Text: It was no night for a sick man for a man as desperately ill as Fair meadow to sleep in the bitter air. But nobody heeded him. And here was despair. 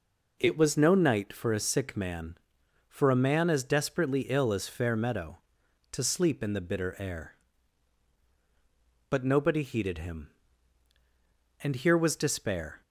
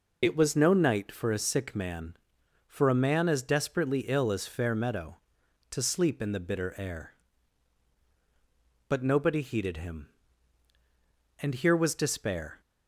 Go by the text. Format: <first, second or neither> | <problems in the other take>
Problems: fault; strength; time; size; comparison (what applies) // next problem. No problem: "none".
first | loses the start of "It"; at 0.2 s; 40 ms